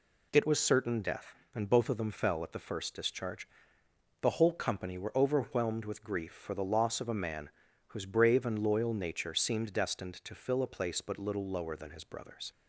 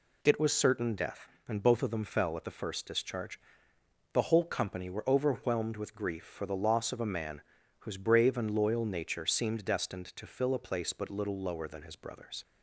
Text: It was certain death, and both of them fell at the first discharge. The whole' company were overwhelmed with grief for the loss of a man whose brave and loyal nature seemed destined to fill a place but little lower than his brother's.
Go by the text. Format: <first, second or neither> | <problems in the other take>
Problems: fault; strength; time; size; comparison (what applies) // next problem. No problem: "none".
neither | pauses between "man" and "whose"; the same in both